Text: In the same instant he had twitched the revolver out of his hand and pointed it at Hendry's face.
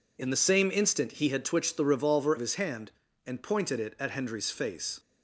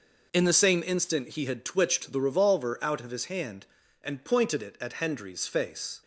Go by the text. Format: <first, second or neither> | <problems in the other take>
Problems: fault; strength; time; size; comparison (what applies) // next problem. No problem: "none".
second | skips "out"; at 2.3 s